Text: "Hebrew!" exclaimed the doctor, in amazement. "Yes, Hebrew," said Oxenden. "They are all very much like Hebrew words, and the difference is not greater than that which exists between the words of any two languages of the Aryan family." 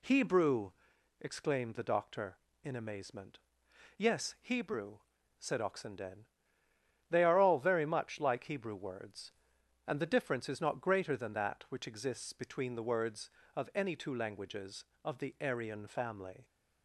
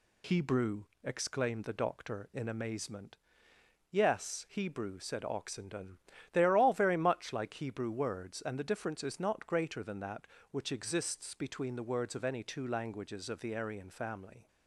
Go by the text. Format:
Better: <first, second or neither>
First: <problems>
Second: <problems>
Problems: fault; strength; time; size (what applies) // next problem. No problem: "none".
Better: neither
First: none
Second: none